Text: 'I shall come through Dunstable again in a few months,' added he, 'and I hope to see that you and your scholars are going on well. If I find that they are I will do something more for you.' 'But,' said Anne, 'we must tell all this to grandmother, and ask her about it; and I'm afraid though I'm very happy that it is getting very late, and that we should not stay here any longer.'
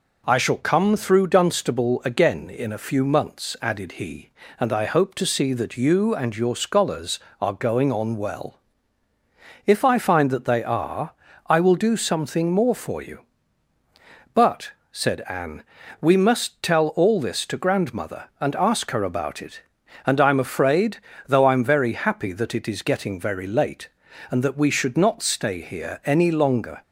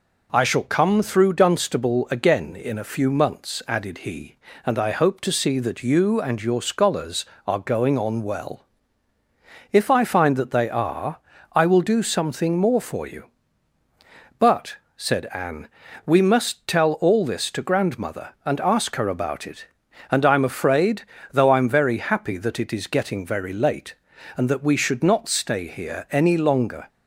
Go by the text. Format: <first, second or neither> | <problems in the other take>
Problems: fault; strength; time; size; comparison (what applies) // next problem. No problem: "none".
neither | pauses between "are" and "I"; slight; the same in both // pauses between "afraid" and "though"; slight; the same in both